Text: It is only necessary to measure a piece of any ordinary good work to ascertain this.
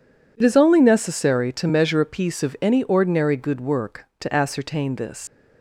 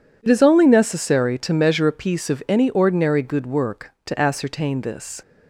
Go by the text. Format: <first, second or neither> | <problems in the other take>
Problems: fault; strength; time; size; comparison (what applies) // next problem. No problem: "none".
second | leaves "this" unfinished; at 5.2 s; 80 ms